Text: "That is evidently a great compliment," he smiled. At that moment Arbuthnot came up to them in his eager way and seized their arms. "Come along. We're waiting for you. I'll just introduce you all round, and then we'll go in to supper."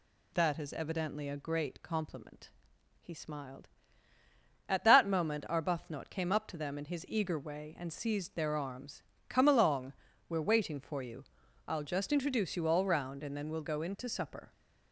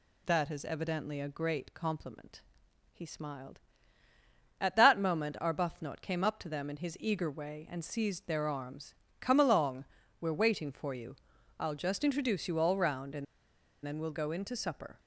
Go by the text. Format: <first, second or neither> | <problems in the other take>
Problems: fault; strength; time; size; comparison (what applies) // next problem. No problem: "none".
first | pauses between "and" and "then"; noticeable; at 13.2 s; 0.60 s long